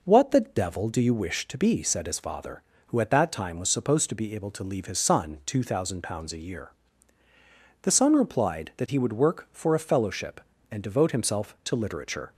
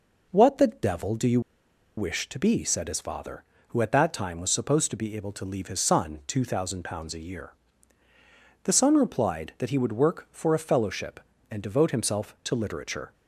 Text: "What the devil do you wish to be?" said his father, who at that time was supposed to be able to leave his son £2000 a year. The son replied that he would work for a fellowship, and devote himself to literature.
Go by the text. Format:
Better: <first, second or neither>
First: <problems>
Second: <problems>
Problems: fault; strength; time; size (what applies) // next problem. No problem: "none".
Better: first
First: none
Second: pauses between "you" and "wish"; noticeable; at 1.3 s; 0.57 s long